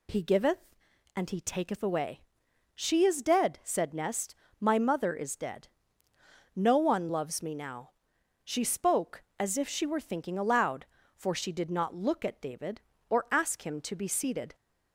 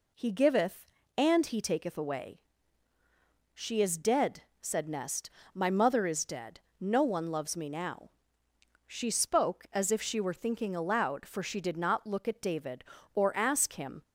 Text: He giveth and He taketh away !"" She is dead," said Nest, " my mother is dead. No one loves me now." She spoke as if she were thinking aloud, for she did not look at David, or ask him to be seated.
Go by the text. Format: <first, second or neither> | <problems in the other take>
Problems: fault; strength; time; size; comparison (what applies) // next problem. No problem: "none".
first | stops before "to be seated"; at 14.0 s